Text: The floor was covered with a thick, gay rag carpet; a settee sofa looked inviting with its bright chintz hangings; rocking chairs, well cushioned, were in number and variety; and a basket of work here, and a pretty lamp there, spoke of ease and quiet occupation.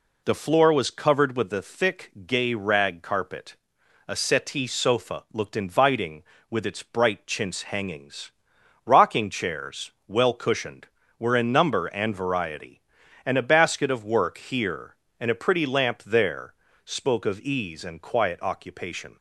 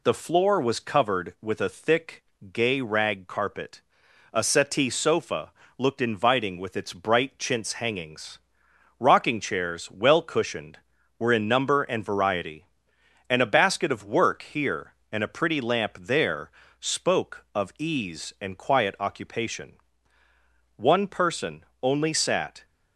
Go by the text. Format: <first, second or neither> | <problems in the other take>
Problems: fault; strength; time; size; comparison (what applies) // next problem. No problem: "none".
first | pauses between "sofa" and "looked"; slight; at 5.5 s; 0.26 s long // goes on to say "One person only sat"; strong; from 20.7 s on; 1.8 s long